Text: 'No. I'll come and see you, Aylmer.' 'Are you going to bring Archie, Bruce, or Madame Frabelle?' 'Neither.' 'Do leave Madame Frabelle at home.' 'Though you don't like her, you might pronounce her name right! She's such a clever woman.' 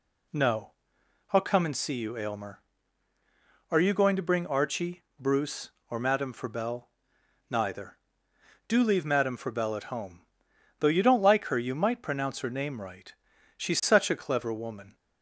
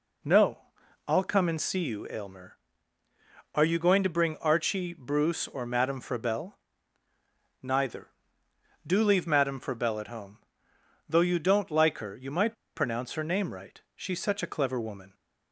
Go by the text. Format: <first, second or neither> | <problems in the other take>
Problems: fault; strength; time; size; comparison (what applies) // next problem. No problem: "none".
first | pauses between "might" and "pronounce"; slight; at 12.5 s; 0.20 s long